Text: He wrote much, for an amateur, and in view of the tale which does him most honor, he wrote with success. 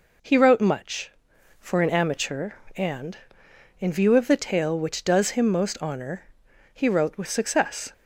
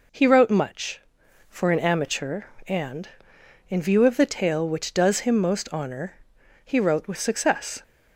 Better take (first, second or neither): neither